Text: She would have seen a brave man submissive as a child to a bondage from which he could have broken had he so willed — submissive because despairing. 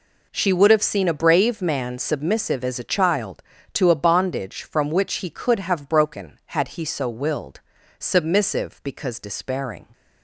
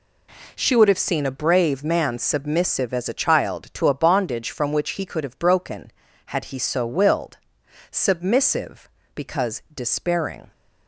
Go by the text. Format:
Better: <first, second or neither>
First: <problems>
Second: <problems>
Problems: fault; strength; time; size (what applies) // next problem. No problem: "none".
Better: neither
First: none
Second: none